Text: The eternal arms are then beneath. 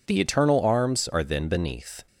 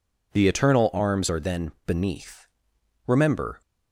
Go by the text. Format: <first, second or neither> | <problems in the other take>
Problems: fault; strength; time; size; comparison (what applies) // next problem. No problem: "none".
first | pauses between "then" and "beneath"; slight; at 1.7 s; 0.16 s long // goes on to say "Remember"; from 3.0 s on; 0.54 s long